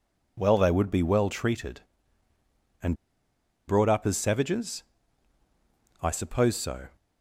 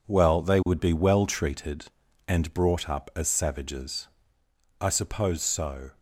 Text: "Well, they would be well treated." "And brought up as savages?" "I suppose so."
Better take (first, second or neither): second